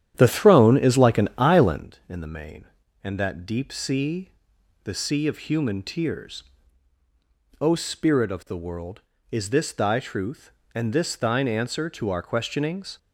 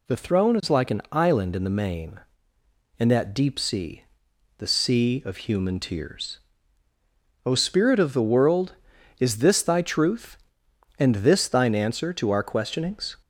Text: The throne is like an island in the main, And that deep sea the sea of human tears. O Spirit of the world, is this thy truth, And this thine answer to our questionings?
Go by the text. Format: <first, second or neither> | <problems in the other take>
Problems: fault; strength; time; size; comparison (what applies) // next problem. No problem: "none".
second | starts louder than the rest; strong; until 1.9 s; 10.5 dB // pauses between "sea" and "the"; noticeable; at 4.3 s; 0.54 s long; noticeable in the second